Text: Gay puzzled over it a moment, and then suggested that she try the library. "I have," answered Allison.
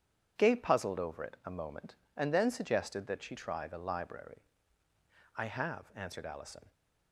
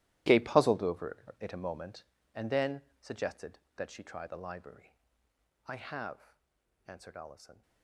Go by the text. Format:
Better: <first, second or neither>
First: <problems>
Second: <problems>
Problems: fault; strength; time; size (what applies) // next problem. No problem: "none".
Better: first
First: starts louder than the rest; strong; until 1.3 s; 8.5 dB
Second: gets quieter; strong; throughout; 15 dB // starts louder than the rest; strong; until 1.5 s; 15 dB // pauses between "over" and "it"; slight; at 1.1 s; 0.24 s long // pauses between "then" and "suggested"; slight; at 2.8 s; 0.18 s long